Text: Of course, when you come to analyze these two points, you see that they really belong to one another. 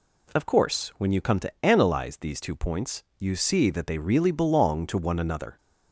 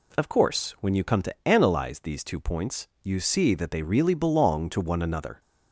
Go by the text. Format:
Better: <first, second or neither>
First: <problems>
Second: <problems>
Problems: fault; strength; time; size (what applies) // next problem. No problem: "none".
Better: neither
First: none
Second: none